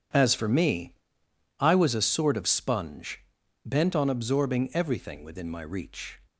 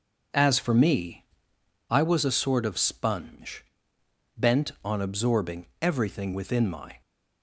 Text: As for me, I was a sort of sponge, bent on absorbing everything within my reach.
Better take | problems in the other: first | starts louder than the rest; until 2.0 s; 6.5 dB // pauses between "absorbing" and "everything"; slight; at 5.6 s; 0.16 s long // stops before "reach"; at 7.0 s

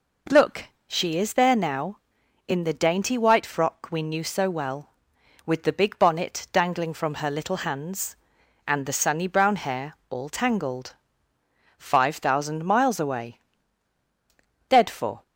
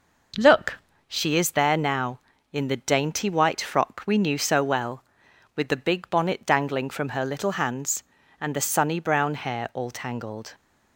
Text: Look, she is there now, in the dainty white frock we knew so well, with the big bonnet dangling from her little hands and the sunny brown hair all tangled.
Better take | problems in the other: second | pauses between "hair" and "all"; slight; at 9.9 s; 0.16 s long // goes on to say "Five thousand miles away Dead for"; strong; from 11.7 s on; 3.4 s long

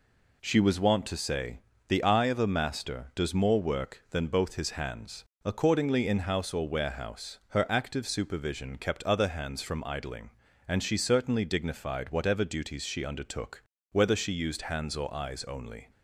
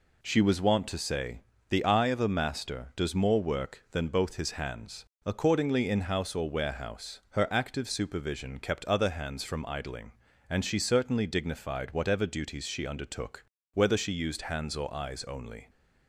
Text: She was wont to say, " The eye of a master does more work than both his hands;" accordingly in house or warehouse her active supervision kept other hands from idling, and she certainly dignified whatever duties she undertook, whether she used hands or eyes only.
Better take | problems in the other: neither | none

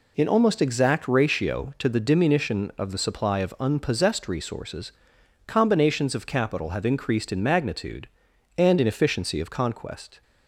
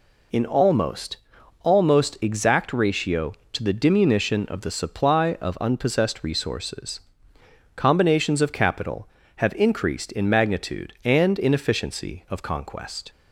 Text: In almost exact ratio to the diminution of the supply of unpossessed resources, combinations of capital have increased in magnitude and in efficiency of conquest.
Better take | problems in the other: first | says "almost" twice; at 1.6 s

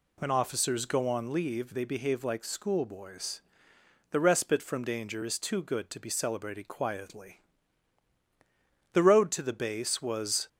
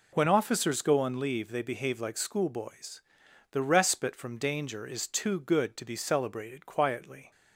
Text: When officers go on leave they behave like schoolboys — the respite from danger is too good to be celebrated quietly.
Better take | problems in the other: second | goes on to say "The road to the base was"; from 8.9 s on; 1.5 s long

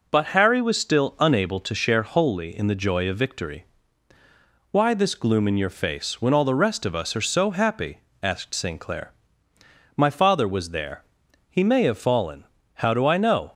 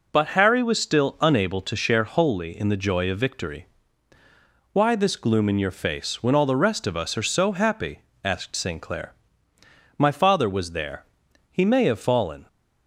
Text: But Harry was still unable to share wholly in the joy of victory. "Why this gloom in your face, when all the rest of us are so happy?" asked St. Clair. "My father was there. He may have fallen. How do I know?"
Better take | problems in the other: first | stops before "How do I know"; at 12.4 s

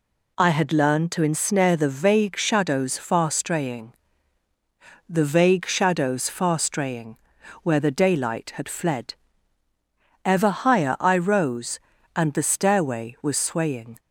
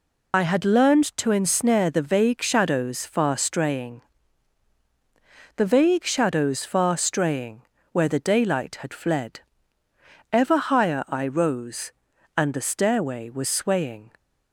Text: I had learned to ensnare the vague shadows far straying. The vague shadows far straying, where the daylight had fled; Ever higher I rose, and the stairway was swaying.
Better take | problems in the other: first | loses the start of "I"; at 0.3 s; 45 ms

